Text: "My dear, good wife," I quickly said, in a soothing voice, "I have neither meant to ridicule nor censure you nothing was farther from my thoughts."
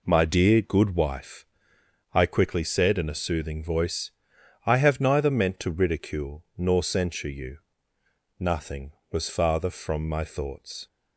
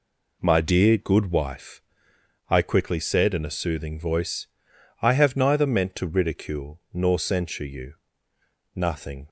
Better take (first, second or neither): first